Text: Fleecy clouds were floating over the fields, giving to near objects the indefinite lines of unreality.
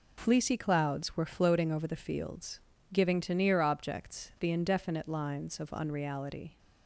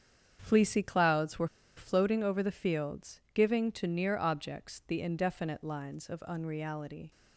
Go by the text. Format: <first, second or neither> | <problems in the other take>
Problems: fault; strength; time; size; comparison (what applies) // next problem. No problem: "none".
first | starts louder than the rest; strong; until 1.4 s; 8 dB // pauses between "were" and "floating"; slight; at 1.4 s; 0.30 s long